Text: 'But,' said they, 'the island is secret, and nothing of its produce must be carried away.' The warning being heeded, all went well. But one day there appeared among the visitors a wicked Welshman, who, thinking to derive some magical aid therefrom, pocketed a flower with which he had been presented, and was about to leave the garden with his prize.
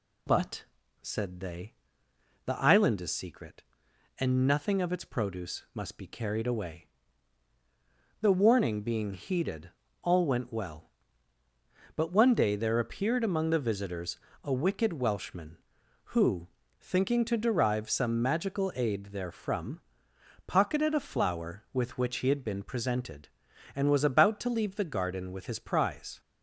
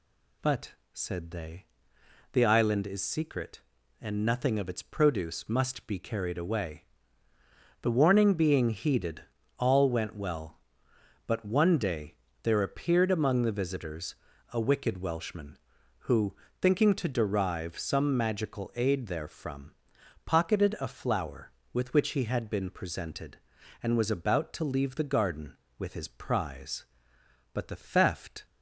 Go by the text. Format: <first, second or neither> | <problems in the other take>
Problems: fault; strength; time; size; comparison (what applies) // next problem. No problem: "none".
first | pauses between "day" and "there"; slight; at 12.1 s; 0.28 s long // pauses between "visitors" and "a"; slight; at 14.1 s; 0.36 s long; slight in the first // goes on to say "But the theft"; noticeable; from 27.5 s on; 0.92 s long